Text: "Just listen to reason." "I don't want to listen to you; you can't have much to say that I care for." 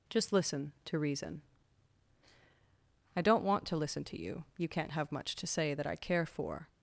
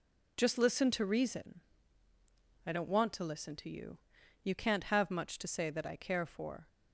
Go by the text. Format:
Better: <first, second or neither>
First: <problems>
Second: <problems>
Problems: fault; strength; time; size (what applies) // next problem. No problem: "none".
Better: neither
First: none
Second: none